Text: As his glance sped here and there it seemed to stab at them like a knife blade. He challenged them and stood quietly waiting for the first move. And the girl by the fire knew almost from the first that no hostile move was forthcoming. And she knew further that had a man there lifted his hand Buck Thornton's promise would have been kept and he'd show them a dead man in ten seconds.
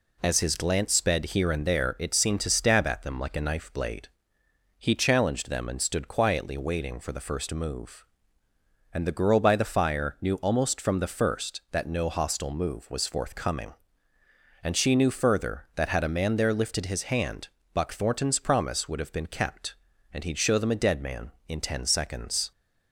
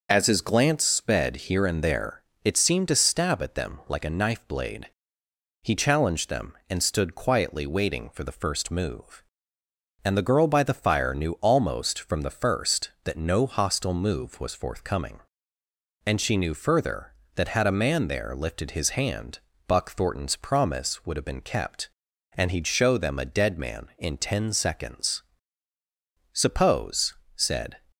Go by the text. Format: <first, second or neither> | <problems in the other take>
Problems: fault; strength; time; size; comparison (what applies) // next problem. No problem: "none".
first | pauses between "there" and "it"; slight; at 2.2 s; 0.20 s long // pauses between "hand" and "Buck"; slight; at 19.3 s; 0.30 s long; slight in the first // goes on to say "Suppose said"; from 26.3 s on; 1.4 s long